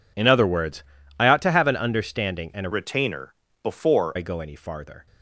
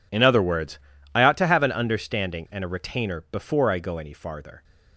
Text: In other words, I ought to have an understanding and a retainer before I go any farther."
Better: second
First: changes voice from "retainer" to "before"; from 2.7 to 4.1 s; 1.4 s long // pauses between "retainer" and "before"; slight; at 3.3 s; 0.28 s long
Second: none

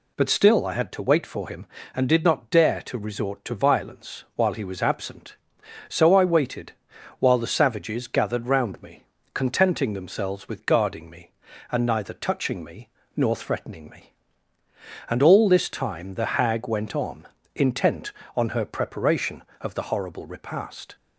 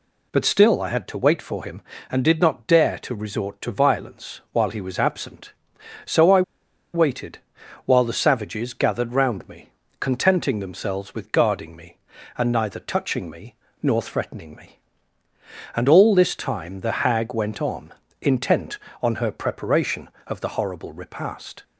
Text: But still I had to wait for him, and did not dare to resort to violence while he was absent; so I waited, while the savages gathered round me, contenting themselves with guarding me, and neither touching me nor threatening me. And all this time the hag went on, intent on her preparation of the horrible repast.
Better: first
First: pauses between "me" and "nor"; slight; at 12.8 s; 0.26 s long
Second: pauses between "I" and "waited"; noticeable; at 6.4 s; 0.52 s long // pauses between "me" and "nor"; slight; at 13.5 s; 0.26 s long

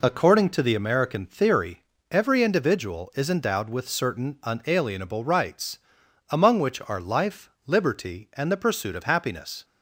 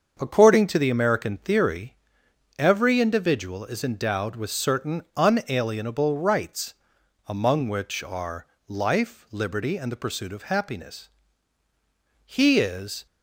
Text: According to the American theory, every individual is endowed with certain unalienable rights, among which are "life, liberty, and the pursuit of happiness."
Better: first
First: none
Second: starts louder than the rest; until 1.2 s; 6.5 dB // pauses between "are" and "life"; slight; at 8.4 s; 0.22 s long // goes on to say "He is"; noticeable; from 12.2 s on; 0.80 s long

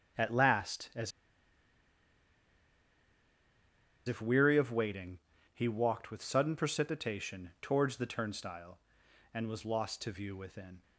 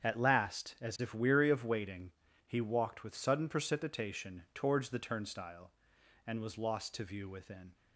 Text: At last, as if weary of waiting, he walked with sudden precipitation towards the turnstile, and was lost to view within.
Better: second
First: starts louder than the rest; strong; until 4.1 s; 7.5 dB // pauses between "as" and "if"; strong; at 1.1 s; 2.9 s long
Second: starts louder than the rest; strong; until 1.0 s; 8 dB

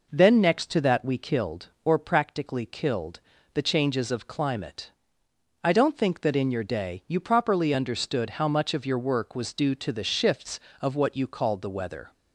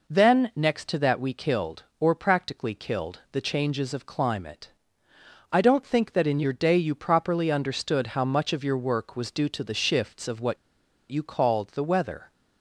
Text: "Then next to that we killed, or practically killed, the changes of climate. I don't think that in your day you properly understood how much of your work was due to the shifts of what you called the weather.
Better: first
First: none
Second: pauses between "what" and "you"; noticeable; at 10.5 s; 0.54 s long

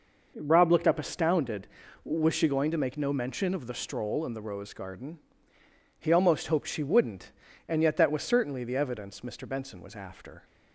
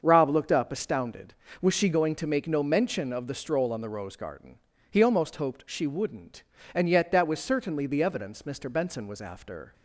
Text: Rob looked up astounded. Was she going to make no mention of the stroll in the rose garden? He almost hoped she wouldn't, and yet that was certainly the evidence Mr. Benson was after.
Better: first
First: none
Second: starts louder than the rest; until 1.0 s; 6.5 dB // says "on" for "in"; at 3.7 s

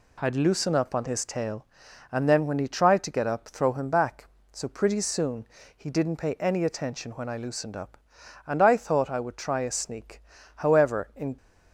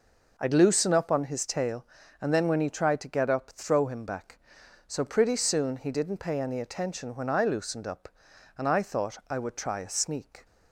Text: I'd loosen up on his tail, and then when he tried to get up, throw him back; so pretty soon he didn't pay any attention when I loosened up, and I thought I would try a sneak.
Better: second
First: pauses between "soon" and "he"; slight; at 5.4 s; 0.30 s long // goes on to say "However in"; noticeable; from 10.5 s on; 0.82 s long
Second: none

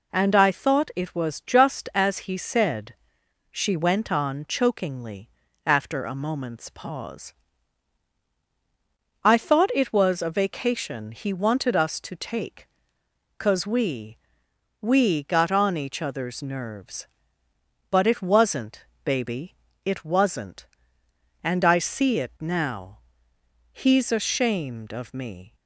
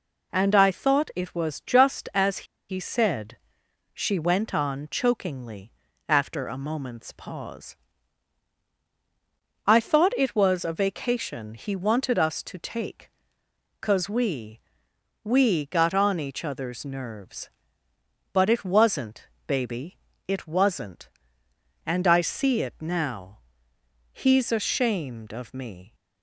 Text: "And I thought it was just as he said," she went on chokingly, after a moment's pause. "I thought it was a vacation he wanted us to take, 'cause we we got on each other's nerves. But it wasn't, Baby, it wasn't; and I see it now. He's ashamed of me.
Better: first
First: pauses between "we" and "we"; noticeable; at 14.1 s; 0.66 s long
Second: pauses between "as" and "he"; slight; at 2.4 s; 0.23 s long // pauses between "we" and "we"; noticeable; at 14.5 s; 0.66 s long

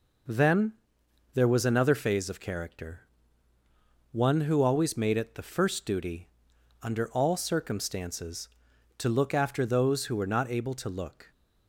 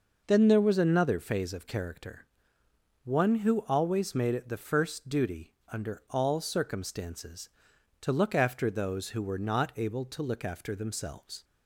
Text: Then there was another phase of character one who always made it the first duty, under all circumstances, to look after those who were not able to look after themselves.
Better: second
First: pauses between "Then" and "there"; noticeable; at 0.7 s; 0.62 s long // pauses between "character" and "one"; at 3.0 s; 1.1 s long // stops before "after themselves"; at 11.3 s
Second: pauses between "character" and "one"; noticeable; at 2.2 s; 0.78 s long

